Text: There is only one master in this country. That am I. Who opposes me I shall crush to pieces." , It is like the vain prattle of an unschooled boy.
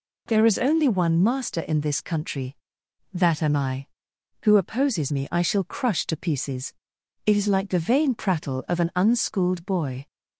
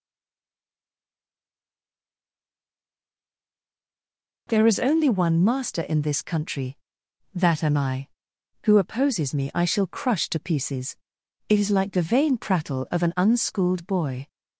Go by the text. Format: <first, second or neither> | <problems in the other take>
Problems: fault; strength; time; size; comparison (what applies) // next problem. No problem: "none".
first | stays silent before the first word; strong; until 4.4 s; 4.4 s long